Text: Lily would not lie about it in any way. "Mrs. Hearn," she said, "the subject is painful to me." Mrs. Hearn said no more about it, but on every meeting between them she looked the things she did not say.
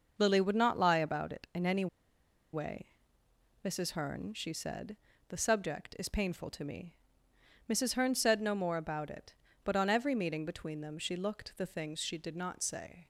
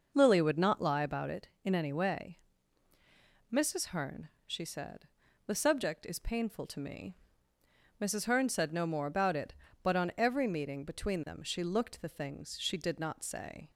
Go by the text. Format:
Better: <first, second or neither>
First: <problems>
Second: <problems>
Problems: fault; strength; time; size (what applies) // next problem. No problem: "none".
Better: second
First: pauses between "any" and "way"; noticeable; at 1.8 s; 0.66 s long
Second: none